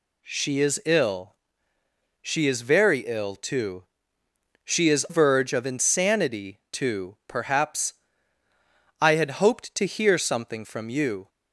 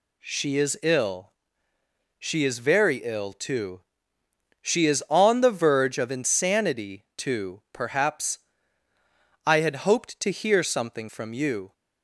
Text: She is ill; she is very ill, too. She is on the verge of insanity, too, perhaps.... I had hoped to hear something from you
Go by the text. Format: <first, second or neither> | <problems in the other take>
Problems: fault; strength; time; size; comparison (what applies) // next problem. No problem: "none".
second | skips "on the"; at 5.0 s